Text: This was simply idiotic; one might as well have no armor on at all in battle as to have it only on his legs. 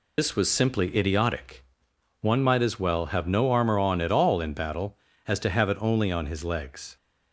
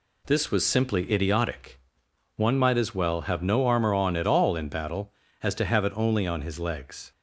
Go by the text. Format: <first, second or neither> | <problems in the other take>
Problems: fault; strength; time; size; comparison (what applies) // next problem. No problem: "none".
second | loses the start of "This"; at 0.1 s; 90 ms